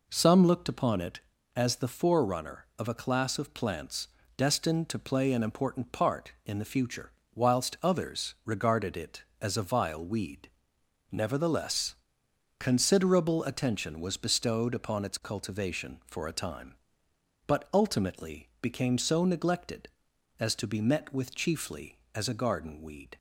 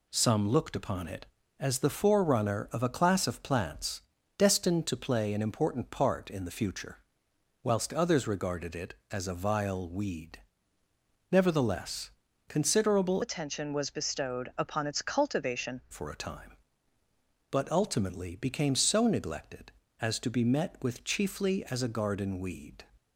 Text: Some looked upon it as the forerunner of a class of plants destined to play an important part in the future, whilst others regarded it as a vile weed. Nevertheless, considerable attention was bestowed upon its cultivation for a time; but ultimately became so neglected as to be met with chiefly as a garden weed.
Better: first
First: pauses between "plants" and "destined"; slight; at 4.0 s; 0.30 s long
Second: pauses between "plants" and "destined"; slight; at 4.0 s; 0.36 s long // changes voice from "attention" to "cultivation"; from 13.2 to 15.8 s; 2.6 s long

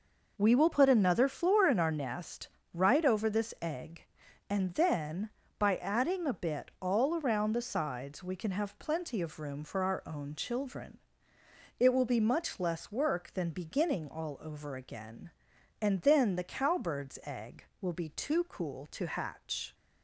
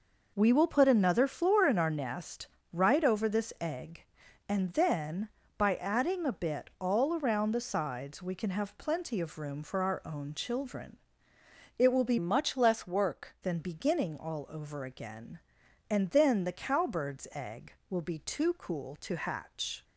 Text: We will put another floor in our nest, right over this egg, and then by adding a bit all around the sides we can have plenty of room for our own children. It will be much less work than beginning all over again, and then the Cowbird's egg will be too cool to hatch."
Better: first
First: none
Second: changes voice from "much" to "work"; from 12.1 to 13.3 s; 1.2 s long

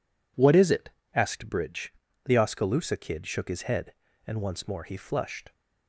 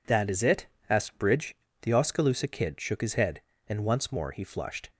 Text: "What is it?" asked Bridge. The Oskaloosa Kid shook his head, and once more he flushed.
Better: first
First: none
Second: says "That" for "What"; at 0.0 s

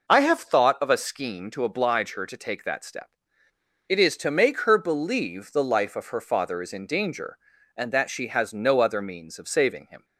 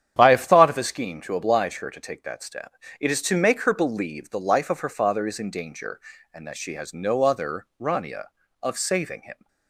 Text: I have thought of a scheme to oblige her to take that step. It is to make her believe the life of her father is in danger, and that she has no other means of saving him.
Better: first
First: none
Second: starts louder than the rest; strong; until 1.2 s; 9.5 dB // says "rania" for "means"; at 7.7 s

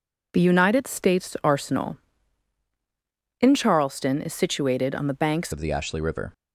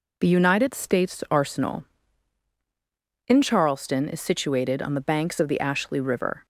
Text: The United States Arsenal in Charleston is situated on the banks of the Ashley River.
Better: second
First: changes voice at "of"; from 5.5 s on; 0.8 s long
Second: none

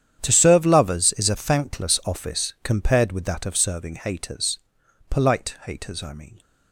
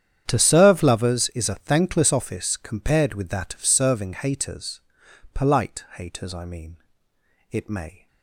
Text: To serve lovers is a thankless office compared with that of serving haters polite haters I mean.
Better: first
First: starts louder than the rest; strong; until 1.2 s; 9.5 dB // pauses between "haters" and "polite"; noticeable; at 4.5 s; 0.50 s long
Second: starts louder than the rest; strong; until 1.2 s; 9 dB // pauses between "haters" and "polite"; noticeable; at 4.8 s; 0.54 s long // goes on to say "It may"; from 7.5 s on; 0.54 s long

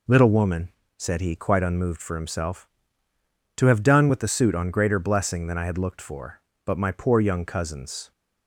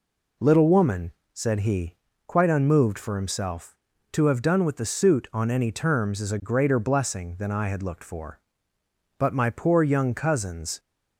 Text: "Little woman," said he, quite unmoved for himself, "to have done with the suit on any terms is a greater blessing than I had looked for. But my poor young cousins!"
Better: second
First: skips "any terms is a"; at 4.6 s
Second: none

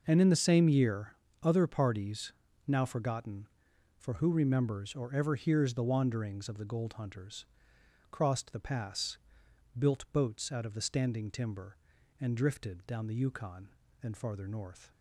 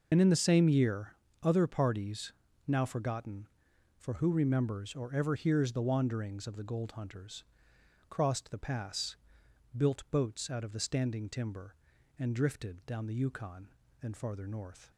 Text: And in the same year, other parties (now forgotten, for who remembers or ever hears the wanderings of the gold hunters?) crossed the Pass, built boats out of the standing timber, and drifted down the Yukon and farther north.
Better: first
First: none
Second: loses the start of "And"; at 0.1 s; 60 ms

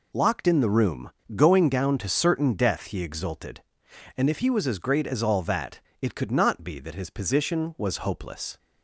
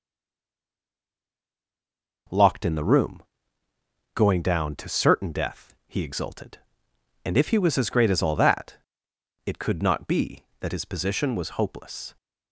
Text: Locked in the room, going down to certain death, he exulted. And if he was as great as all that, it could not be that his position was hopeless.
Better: first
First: none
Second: stays silent before the first word; until 2.2 s; 2.2 s long

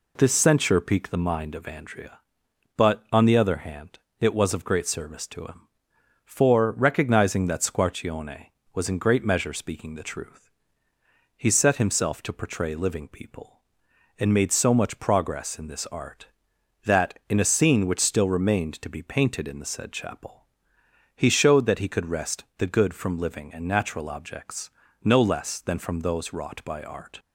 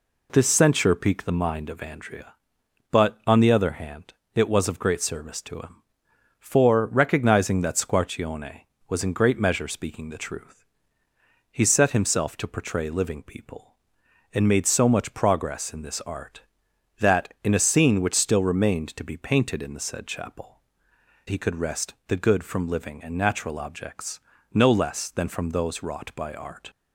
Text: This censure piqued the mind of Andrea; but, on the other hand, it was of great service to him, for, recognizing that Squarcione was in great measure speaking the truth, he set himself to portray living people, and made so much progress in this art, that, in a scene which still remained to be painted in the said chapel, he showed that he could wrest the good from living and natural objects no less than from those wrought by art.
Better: first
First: pauses between "objects" and "no"; slight; at 24.7 s; 0.34 s long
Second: skips "he showed that"; at 20.9 s // pauses between "objects" and "no"; slight; at 24.1 s; 0.34 s long

